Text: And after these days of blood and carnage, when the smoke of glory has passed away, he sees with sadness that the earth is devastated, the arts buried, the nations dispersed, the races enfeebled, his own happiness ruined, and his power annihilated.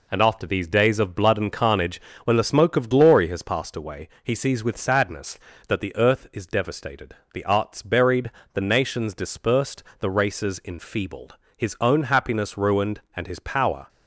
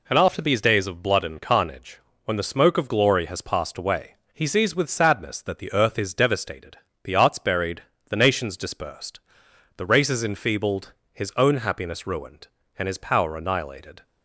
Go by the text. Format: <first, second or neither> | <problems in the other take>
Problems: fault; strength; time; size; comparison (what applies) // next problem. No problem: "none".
second | stops before "annihilated"; at 13.8 s